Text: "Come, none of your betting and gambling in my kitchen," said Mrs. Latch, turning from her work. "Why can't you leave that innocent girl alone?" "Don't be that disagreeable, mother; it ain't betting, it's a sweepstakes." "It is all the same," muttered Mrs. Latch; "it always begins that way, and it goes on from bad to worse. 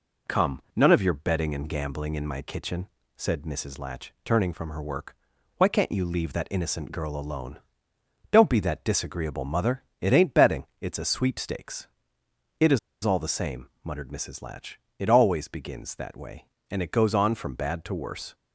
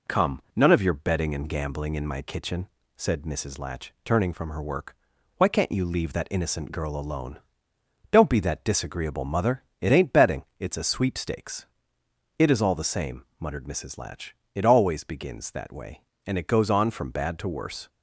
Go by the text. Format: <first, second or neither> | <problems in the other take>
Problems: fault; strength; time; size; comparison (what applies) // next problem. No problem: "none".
second | pauses between "is" and "all"; slight; at 12.7 s; 0.25 s long